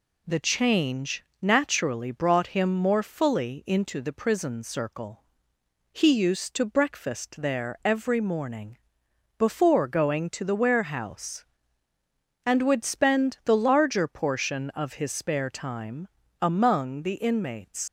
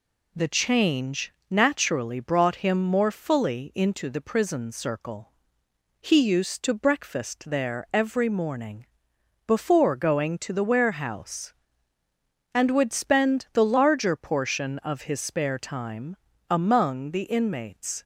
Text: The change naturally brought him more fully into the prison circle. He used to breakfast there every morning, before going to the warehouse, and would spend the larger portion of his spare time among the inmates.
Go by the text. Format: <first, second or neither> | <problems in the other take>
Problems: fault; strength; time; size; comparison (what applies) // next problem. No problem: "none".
second | pauses between "change" and "naturally"; slight; at 1.2 s; 0.20 s long; slight in the second // pauses between "time" and "among"; slight; at 16.0 s; 0.32 s long; slight in the second // leaves "inmates" unfinished; at 17.8 s; 60 ms